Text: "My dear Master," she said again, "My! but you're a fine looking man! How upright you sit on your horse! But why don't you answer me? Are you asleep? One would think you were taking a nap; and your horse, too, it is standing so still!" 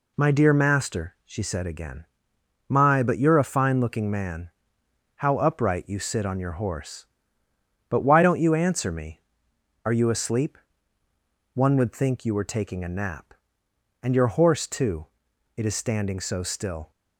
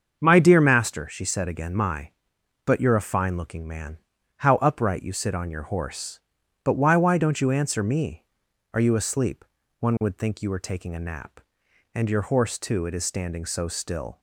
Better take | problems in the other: first | starts louder than the rest; until 1.2 s; 6.5 dB // says "why" twice; at 6.9 s

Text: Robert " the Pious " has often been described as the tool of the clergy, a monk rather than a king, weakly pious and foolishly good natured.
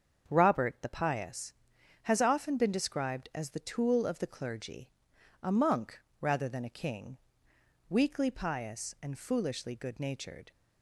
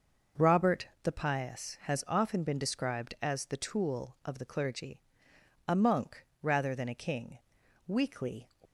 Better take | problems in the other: first | starts louder than the rest; until 1.4 s; 6 dB; also in the first // pauses between "monk" and "rather"; slight; at 6.2 s; 0.16 s long; slight in the first // stops before "pious and foolishly good natured"; at 8.6 s

